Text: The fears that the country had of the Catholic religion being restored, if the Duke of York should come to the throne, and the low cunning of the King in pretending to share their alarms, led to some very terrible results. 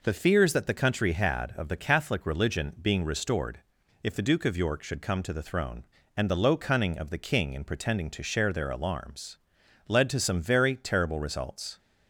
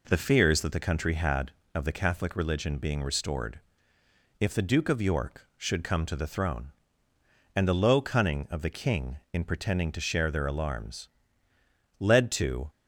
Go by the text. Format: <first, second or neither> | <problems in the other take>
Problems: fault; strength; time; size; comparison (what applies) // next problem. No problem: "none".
first | stops before "some very terrible results"; at 12.6 s